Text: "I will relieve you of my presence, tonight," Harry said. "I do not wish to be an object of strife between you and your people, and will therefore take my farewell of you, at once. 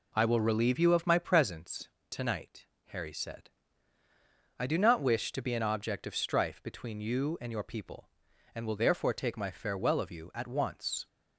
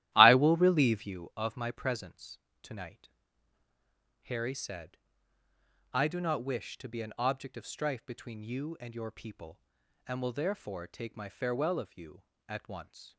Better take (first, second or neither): first